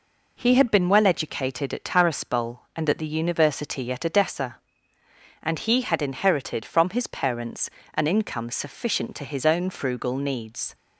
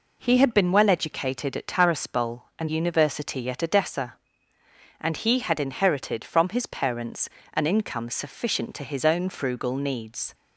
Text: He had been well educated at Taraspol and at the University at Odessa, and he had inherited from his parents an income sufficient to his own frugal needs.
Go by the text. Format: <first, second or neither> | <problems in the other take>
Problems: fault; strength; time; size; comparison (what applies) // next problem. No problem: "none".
first | skips "at the"; at 2.6 s // pauses between "parents" and "an"; slight; at 7.2 s; 0.24 s long; slight in the first